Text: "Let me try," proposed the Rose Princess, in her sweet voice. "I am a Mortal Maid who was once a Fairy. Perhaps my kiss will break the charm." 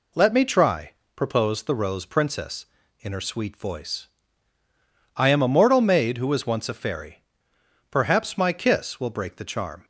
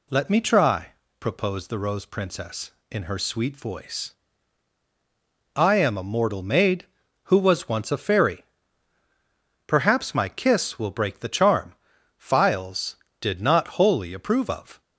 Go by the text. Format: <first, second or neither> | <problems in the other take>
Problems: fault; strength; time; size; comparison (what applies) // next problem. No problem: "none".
first | goes on to say "Files did not wholly approve of"; strong; from 12.1 s on; 2.6 s long